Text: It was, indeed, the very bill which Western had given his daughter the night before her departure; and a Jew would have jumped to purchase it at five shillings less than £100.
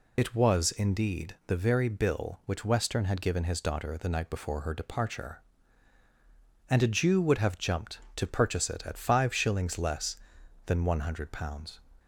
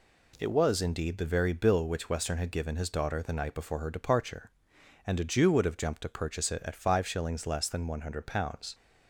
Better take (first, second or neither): second